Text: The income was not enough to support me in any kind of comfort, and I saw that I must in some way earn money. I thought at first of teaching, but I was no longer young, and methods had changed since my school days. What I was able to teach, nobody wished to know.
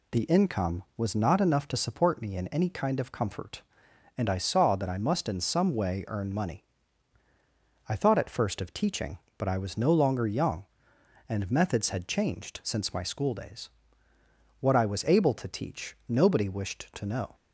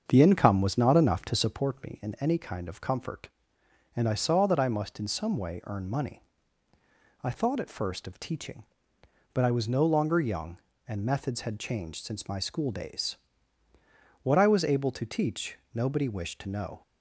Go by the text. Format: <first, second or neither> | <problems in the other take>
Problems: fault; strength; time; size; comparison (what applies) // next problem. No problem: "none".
first | starts louder than the rest; strong; until 1.6 s; 7 dB